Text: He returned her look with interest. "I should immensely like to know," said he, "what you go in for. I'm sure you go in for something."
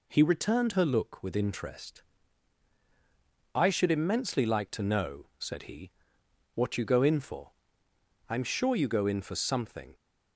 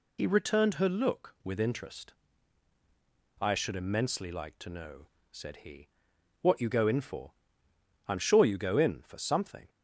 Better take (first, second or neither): first